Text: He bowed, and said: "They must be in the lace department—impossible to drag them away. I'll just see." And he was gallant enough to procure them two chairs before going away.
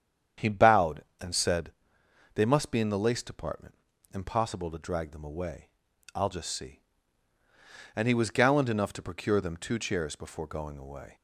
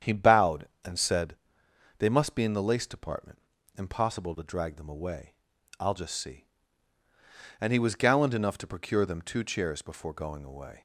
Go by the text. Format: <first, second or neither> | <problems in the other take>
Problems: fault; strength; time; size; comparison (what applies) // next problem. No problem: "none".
neither | starts louder than the rest; strong; the same in both